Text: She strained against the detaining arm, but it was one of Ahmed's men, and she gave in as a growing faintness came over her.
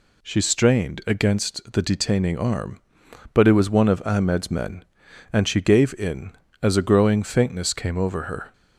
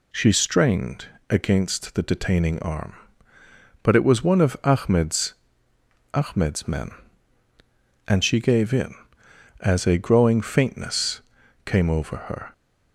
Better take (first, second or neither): first